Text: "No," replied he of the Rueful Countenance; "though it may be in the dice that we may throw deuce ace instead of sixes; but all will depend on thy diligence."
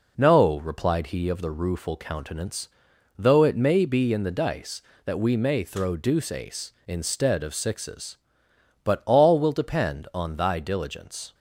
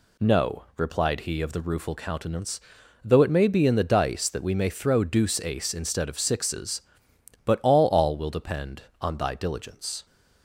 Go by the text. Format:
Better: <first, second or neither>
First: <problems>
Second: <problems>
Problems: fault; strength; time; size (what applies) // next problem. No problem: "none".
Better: first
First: none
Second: says "all" twice; at 7.8 s